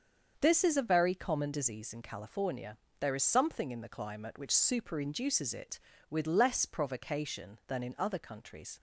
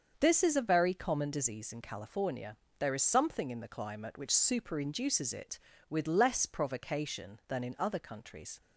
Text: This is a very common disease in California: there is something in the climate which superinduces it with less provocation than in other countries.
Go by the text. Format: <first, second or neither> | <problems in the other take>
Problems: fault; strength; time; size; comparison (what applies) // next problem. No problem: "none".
neither | starts louder than the rest; the same in both